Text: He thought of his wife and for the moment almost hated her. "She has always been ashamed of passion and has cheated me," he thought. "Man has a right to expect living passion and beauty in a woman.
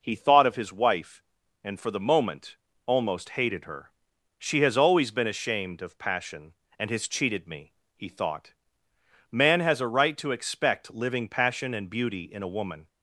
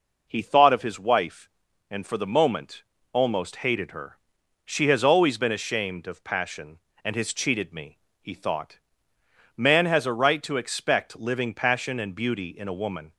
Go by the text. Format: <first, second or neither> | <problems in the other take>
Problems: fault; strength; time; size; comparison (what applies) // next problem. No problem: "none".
neither | pauses between "moment" and "almost"; slight; the same in both